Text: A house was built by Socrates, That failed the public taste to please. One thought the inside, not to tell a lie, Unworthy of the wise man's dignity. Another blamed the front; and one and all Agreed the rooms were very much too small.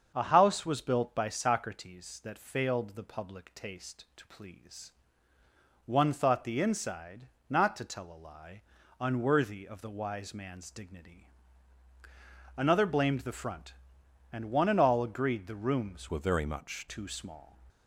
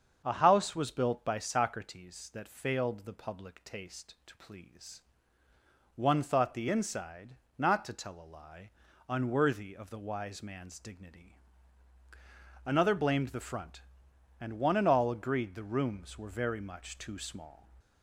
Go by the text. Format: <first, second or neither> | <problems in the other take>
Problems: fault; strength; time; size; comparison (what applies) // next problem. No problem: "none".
second | starts louder than the rest; until 1.1 s; 7 dB; also in the second // changes voice from "were" to "much"; from 16.1 to 16.8 s; 0.7 s long